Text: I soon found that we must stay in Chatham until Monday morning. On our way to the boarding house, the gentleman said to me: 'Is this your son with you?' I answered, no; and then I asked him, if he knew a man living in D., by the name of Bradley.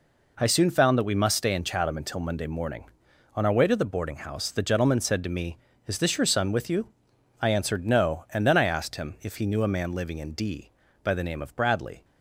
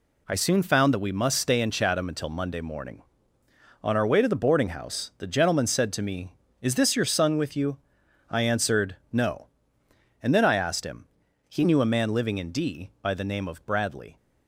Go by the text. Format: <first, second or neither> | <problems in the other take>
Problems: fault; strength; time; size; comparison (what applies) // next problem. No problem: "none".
first | skips "if"; at 11.2 s